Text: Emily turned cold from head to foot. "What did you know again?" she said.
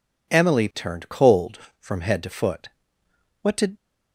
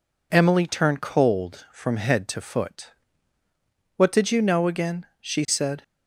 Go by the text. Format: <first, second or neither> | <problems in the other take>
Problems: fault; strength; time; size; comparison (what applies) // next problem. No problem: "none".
second | stops before "you know again she said"; at 3.7 s